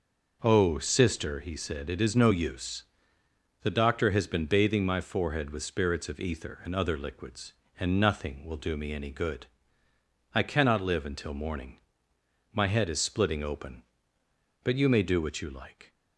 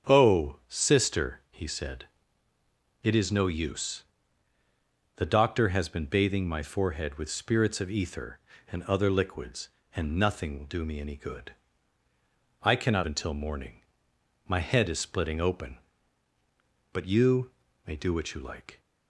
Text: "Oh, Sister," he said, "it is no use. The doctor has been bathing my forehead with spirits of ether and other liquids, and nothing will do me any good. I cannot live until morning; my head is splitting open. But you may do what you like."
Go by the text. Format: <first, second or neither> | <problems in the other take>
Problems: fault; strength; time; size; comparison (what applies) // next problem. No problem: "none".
first | starts louder than the rest; until 1.1 s; 7 dB // skips "live"; at 13.0 s // pauses between "you" and "may"; slight; at 17.4 s; 0.34 s long